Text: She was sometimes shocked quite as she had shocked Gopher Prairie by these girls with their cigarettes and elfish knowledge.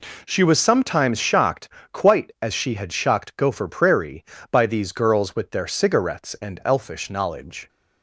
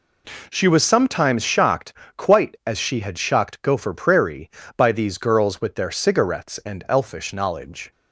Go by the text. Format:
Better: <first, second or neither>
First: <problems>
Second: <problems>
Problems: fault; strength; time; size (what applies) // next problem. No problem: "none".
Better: neither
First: pauses between "shocked" and "quite"; slight; at 1.6 s; 0.22 s long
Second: pauses between "shocked" and "quite"; slight; at 1.9 s; 0.22 s long